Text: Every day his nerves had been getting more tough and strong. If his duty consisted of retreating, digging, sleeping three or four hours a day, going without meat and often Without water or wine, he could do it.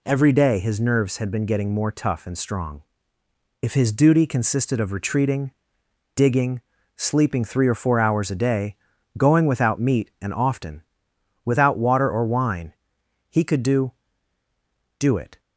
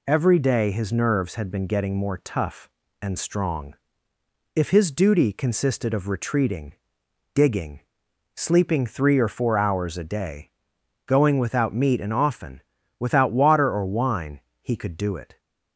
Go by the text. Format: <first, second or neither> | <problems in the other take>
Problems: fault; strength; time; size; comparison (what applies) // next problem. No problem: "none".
second | pauses between "often" and "Without"; noticeable; at 10.8 s; 0.62 s long; also in the second // says "do" twice; at 14.9 s